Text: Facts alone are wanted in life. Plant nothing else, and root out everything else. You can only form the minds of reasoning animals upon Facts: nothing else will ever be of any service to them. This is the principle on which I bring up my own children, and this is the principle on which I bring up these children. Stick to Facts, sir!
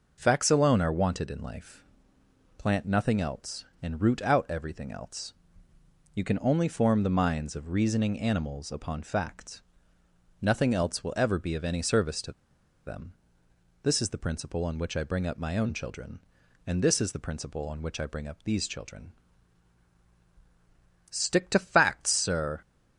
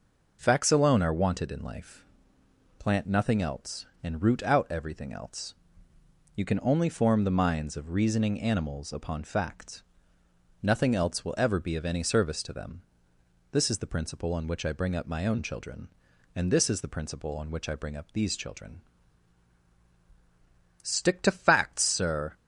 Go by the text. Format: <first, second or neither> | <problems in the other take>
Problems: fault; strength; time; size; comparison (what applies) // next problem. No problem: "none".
second | pauses between "to" and "them"; noticeable; at 12.3 s; 0.52 s long